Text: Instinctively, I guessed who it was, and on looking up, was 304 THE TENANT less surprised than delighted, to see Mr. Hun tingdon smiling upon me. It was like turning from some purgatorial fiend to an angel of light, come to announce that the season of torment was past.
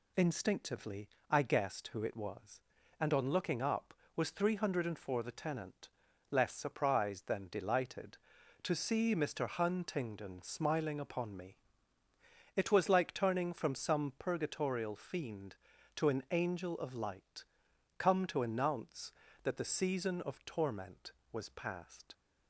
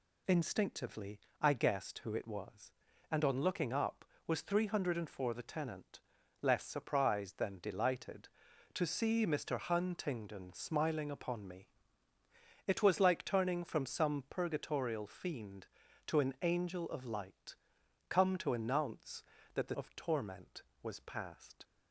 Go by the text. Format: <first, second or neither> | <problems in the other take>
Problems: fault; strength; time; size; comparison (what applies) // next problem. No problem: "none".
first | pauses between "TENANT" and "less"; at 6.0 s; 0.40 s long; also in the first // skips "season"; at 19.7 s